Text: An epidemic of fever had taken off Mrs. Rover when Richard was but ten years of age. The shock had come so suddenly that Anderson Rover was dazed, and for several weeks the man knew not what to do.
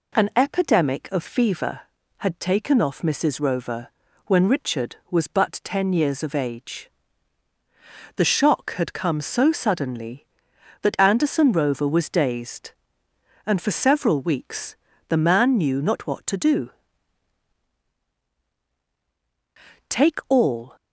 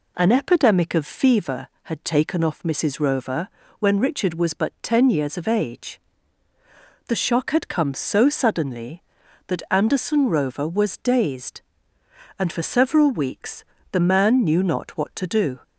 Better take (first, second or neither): second